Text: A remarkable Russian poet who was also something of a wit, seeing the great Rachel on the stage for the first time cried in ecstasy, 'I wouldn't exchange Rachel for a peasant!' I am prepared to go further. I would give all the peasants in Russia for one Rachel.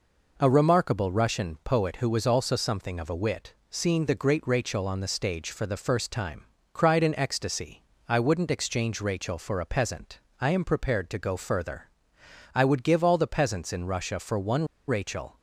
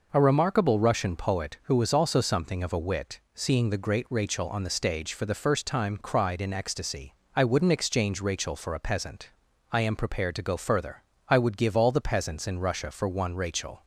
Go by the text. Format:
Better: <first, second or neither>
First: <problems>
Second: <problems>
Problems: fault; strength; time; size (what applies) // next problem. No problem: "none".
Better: second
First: pauses between "time" and "cried"; slight; at 6.4 s; 0.30 s long // pauses between "one" and "Rachel"; slight; at 14.6 s; 0.21 s long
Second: none